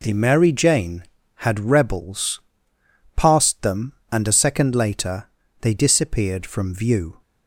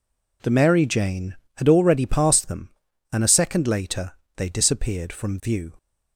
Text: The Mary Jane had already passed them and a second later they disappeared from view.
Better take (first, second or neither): second